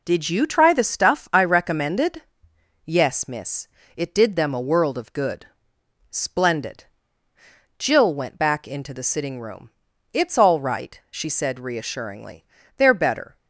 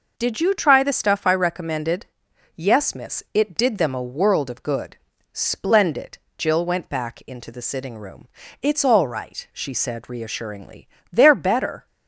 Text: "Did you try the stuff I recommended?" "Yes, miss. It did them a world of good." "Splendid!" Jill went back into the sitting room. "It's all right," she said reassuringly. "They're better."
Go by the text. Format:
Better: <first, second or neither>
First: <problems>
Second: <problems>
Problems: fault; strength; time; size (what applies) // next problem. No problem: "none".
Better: neither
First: none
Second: none